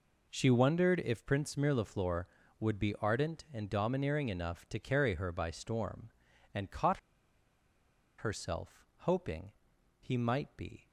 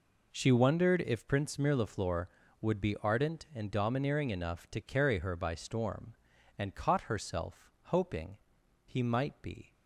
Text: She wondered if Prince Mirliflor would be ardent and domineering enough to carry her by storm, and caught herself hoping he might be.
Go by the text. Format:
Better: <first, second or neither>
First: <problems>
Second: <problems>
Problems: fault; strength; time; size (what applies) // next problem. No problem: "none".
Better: second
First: pauses between "caught" and "herself"; at 6.9 s; 1.1 s long // pauses between "hoping" and "he"; noticeable; at 9.5 s; 0.50 s long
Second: pauses between "hoping" and "he"; noticeable; at 8.3 s; 0.50 s long